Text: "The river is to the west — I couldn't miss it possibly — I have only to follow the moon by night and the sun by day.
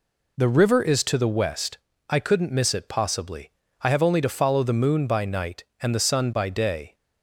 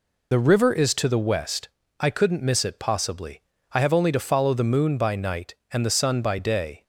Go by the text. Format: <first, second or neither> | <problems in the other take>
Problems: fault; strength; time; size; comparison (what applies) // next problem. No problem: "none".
first | loses the start of "The"; at 0.3 s; 30 ms